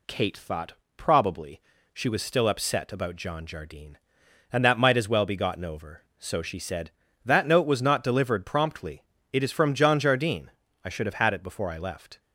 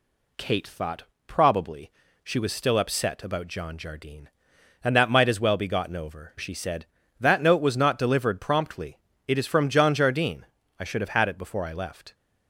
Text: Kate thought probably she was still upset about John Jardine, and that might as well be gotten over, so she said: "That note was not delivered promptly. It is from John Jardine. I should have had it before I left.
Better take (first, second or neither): first